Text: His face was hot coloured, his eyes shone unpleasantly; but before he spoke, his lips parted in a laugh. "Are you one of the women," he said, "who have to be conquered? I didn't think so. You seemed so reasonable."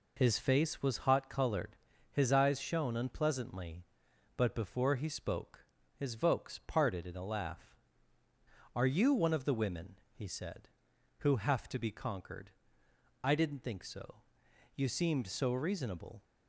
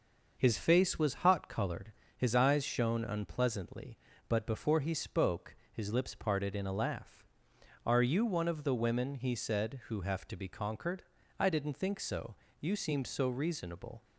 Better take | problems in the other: second | says "vokes" for "lips"; at 6.1 s

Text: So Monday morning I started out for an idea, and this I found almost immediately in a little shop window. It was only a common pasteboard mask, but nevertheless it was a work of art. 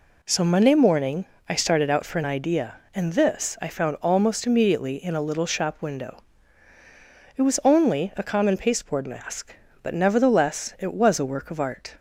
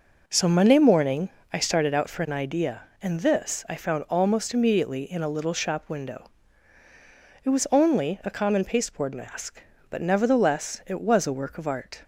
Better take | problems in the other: first | starts louder than the rest; noticeable; until 1.6 s; 5 dB // pauses between "morning" and "I"; slight; at 1.2 s; 0.22 s long; slight in the first

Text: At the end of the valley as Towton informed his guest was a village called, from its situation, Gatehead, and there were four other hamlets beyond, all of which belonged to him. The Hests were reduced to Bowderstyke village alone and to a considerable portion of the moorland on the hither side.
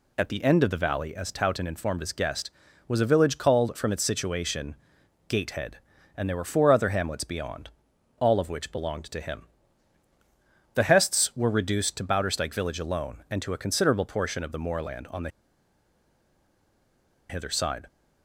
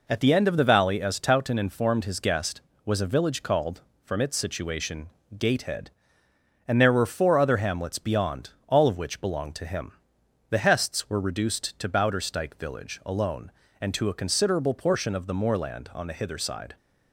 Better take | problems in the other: second | pauses between "the" and "hither"; strong; at 15.2 s; 1.9 s long

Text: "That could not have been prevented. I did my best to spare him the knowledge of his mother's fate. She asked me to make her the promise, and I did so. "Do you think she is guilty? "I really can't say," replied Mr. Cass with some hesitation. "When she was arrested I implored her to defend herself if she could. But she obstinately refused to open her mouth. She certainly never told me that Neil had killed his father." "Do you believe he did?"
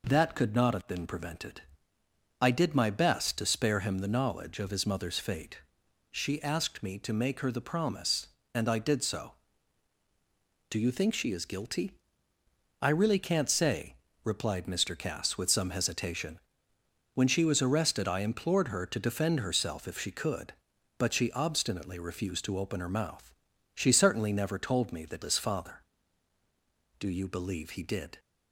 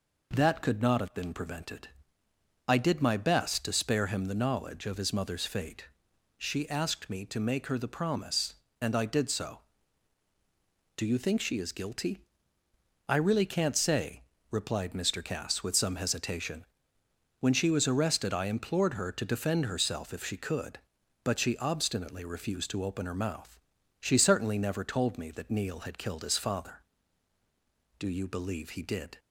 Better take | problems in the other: second | skips "Neil had killed"; at 25.2 s

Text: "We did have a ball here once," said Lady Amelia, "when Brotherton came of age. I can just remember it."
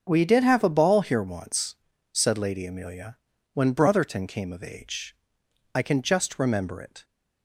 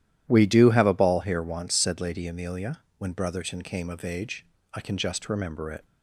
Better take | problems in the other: first | starts louder than the rest; strong; until 1.2 s; 12 dB; also in the first // says "do" for "did"; at 0.4 s

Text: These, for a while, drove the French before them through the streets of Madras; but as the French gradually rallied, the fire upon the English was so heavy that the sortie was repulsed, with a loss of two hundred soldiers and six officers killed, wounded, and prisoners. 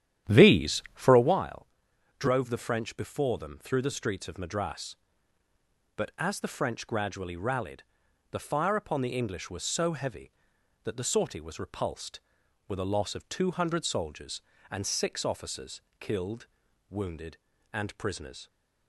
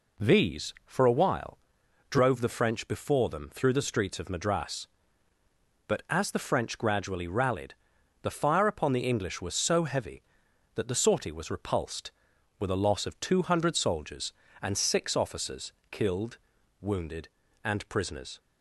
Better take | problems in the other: second | starts louder than the rest; strong; until 1.4 s; 11 dB // pauses between "officers" and "killed"; slight; at 15.8 s; 0.18 s long; slight in the second

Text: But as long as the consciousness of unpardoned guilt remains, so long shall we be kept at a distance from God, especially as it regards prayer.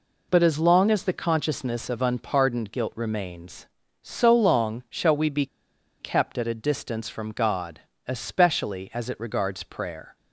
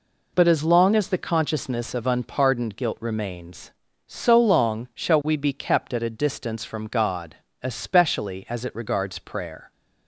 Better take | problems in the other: second | pauses between "be" and "kept"; noticeable; at 5.4 s; 0.54 s long

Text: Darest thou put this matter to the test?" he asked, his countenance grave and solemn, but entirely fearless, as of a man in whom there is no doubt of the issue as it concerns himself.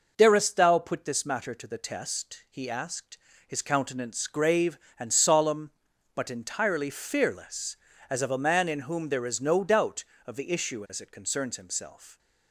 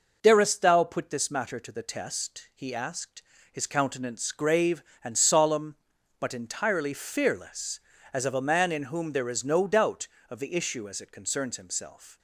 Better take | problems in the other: neither | none

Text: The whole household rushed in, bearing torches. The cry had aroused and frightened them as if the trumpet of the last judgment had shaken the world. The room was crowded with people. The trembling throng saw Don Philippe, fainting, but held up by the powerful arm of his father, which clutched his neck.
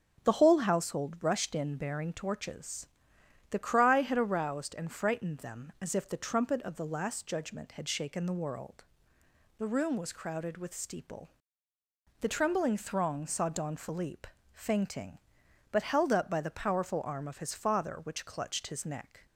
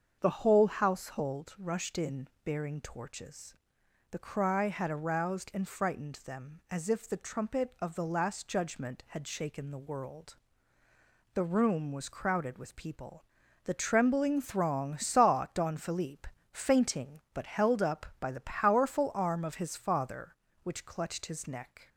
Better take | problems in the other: second | starts louder than the rest; strong; until 1.3 s; 8.5 dB; also in the second // says "steeple" for "people"; at 10.7 s

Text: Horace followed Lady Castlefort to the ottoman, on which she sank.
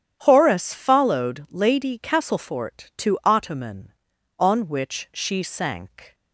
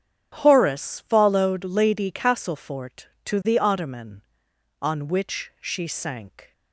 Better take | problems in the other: second | starts louder than the rest; strong; until 1.2 s; 9.5 dB; strong in the second // skips "the"; at 3.2 s

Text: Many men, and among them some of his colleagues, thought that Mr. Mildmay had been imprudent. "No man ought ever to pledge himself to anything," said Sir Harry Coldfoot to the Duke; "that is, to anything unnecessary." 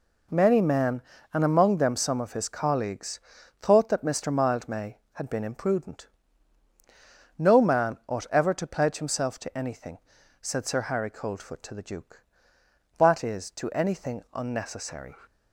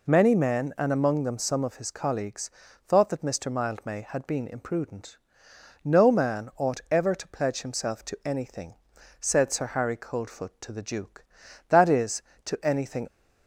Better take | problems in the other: first | stops before "unnecessary"; at 13.0 s

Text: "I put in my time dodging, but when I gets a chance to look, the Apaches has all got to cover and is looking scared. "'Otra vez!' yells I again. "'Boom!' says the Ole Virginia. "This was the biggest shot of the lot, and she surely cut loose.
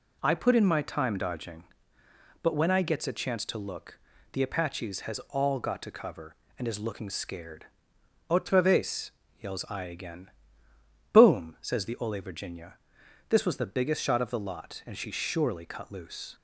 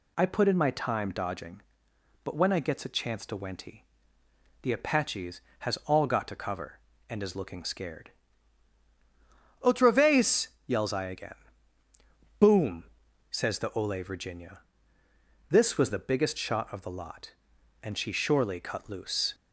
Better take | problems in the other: first | says "wenty" for "look"; at 3.3 s

